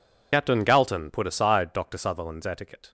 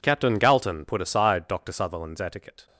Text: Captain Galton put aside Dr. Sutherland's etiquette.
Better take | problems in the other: second | loses the start of "Captain"; at 0.3 s; 45 ms

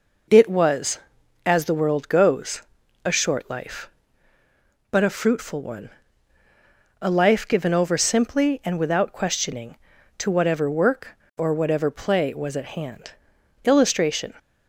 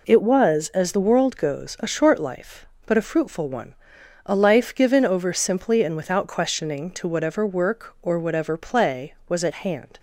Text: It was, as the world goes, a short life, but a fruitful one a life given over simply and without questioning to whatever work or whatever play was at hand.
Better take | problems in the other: second | pauses between "one" and "a"; at 5.8 s; 1.1 s long; noticeable in the second // goes on to say "Illustration"; noticeable; from 13.6 s on; 0.70 s long

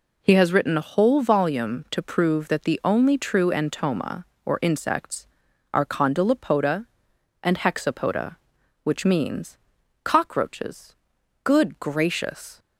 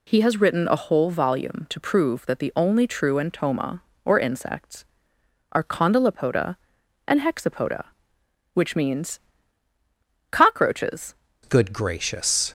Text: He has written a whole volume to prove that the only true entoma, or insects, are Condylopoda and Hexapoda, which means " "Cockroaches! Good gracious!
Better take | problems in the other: first | changes voice at "Good"; from 11.4 s on; 1.1 s long

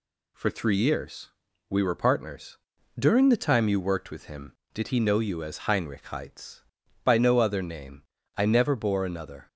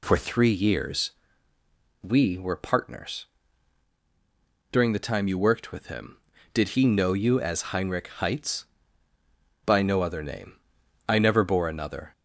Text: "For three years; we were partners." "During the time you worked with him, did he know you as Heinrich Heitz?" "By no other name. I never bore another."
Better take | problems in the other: neither | none

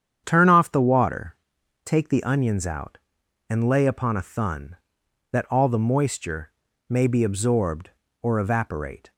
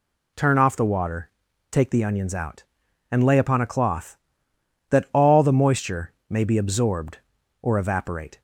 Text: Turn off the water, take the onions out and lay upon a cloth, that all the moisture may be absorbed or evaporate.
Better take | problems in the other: second | starts louder than the rest; strong; until 1.2 s; 8.5 dB // says "thun" for "cloth"; at 4.2 s // pauses between "moisture" and "may"; slight; at 6.5 s; 0.36 s long; slight in the second

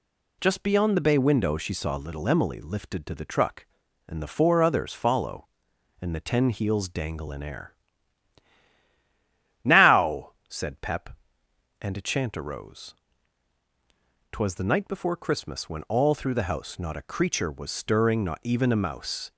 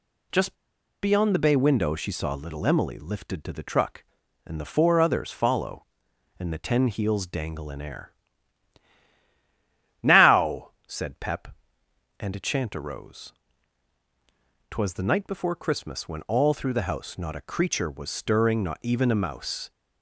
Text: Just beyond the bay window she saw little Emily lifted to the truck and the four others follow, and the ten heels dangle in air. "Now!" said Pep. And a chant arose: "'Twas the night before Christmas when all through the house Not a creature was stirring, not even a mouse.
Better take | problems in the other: first | pauses between "Just" and "beyond"; noticeable; at 0.5 s; 0.48 s long

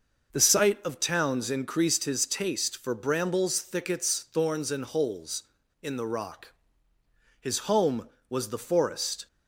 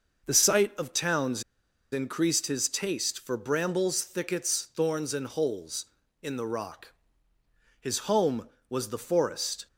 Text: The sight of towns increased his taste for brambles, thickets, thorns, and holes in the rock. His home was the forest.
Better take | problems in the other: first | starts louder than the rest; noticeable; until 1.3 s; 6 dB; noticeable in the first // pauses between "towns" and "increased"; noticeable; at 1.4 s; 0.49 s long

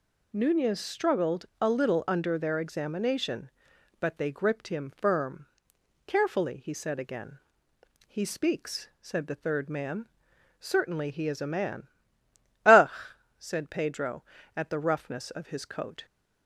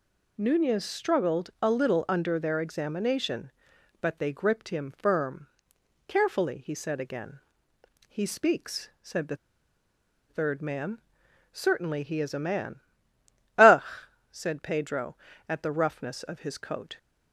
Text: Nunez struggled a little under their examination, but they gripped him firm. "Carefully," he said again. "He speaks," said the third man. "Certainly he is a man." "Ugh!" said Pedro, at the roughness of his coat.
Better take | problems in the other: first | pauses between "the" and "third"; noticeable; at 9.3 s; 0.93 s long

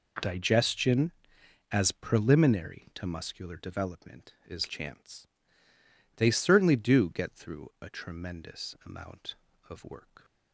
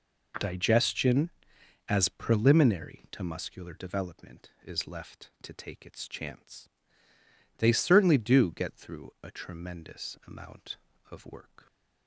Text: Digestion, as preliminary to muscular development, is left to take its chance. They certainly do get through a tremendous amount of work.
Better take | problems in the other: second | skips "left to take its"; at 4.6 s

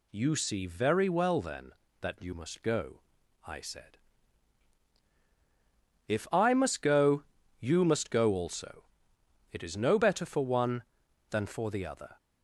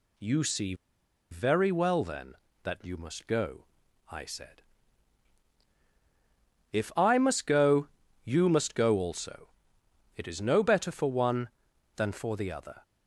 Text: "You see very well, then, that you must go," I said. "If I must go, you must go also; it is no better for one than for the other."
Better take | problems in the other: first | pauses between "see" and "very"; noticeable; at 0.7 s; 0.56 s long

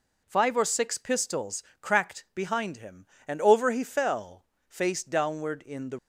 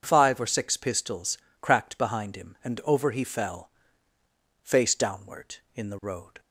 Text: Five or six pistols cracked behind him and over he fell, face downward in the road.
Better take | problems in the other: second | pauses between "pistols" and "cracked"; slight; at 1.6 s; 0.18 s long; slight in the second // stops before "road"; at 5.9 s

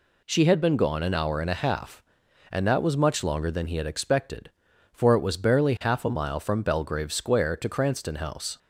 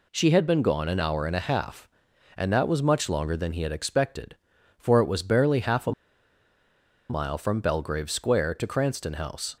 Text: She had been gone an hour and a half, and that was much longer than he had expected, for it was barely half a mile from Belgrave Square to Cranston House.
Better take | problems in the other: first | pauses between "a" and "mile"; at 5.9 s; 1.1 s long

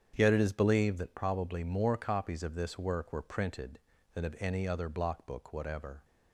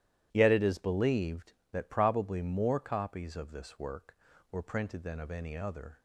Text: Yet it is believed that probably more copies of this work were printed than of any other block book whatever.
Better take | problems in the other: first | starts louder than the rest; strong; until 1.3 s; 13 dB; strong in the first // stops before "block book whatever"; at 5.9 s

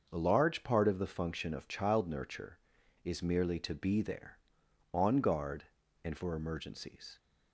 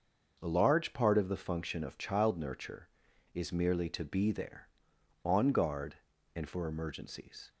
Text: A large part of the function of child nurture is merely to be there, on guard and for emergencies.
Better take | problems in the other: neither | starts louder than the rest; the same in both

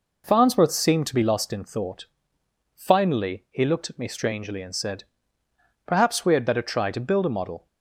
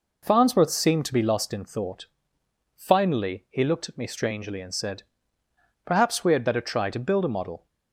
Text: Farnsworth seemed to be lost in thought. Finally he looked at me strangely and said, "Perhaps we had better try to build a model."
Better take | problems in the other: neither | none

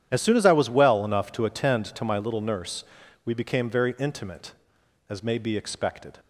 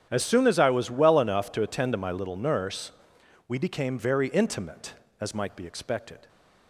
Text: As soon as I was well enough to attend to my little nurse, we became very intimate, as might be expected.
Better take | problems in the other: second | starts louder than the rest; strong; until 1.1 s; 9.5 dB; strong in the second // says "may" for "might"; at 5.2 s

